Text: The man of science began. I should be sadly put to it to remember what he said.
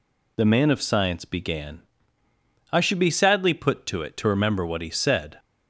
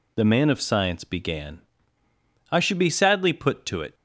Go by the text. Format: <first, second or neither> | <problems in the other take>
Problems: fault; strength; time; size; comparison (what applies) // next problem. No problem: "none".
first | stops before "to remember what he said"; at 3.9 s